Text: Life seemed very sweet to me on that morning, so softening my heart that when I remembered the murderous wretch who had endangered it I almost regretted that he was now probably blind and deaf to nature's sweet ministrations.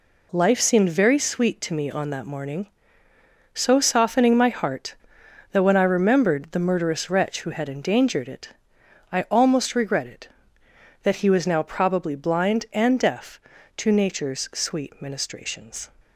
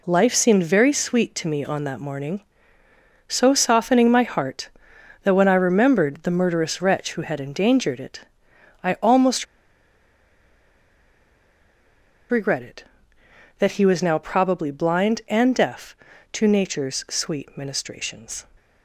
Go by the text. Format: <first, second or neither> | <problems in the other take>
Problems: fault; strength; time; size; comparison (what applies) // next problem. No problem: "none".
first | pauses between "it" and "I"; noticeable; at 8.2 s; 0.62 s long; noticeable in the first // pauses between "almost" and "regretted"; strong; at 9.4 s; 2.8 s long